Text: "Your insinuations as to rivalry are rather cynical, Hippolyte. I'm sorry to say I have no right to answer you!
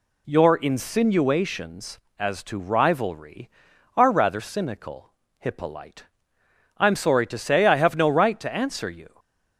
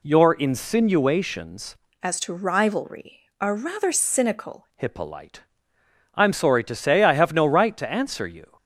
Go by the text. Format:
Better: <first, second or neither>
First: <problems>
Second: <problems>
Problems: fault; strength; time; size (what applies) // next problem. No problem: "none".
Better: first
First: none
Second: changes voice from "as" to "cynical"; from 2.0 to 4.6 s; 2.6 s long